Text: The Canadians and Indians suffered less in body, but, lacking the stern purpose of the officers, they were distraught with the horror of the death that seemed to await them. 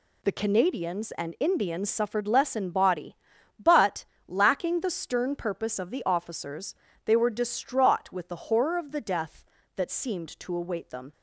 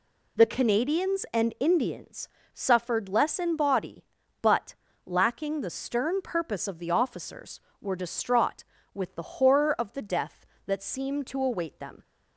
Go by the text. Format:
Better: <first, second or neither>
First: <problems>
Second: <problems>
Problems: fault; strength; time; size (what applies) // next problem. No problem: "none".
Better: first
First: none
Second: pauses between "Indians" and "suffered"; slight; at 2.2 s; 0.24 s long // skips "they"; at 7.6 s